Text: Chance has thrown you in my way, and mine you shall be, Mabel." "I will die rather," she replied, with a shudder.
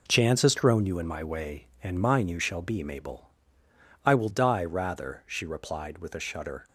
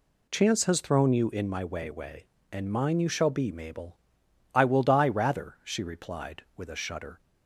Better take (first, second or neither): first